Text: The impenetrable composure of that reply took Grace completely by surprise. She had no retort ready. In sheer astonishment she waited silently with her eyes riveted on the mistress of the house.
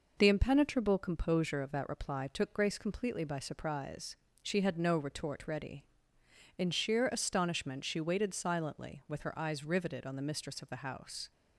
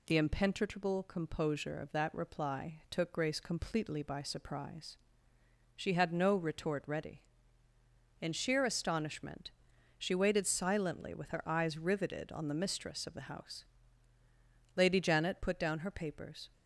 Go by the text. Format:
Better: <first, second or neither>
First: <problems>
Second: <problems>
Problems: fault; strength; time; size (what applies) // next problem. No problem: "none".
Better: first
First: none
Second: pauses between "astonishment" and "she"; noticeable; at 9.5 s; 0.48 s long // goes on to say "Lady Janet put down her papers"; strong; from 14.7 s on; 1.7 s long